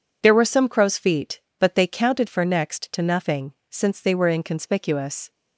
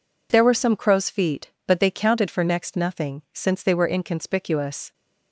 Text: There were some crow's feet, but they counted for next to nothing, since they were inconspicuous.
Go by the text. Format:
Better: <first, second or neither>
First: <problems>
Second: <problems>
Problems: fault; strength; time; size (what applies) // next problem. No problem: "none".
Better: first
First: none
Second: skips "to"; at 2.7 s